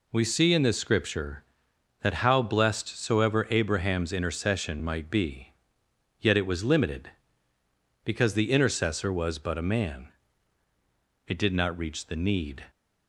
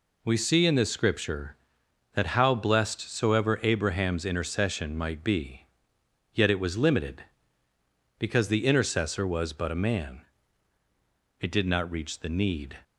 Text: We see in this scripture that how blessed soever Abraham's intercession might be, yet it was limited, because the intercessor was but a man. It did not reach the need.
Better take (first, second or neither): neither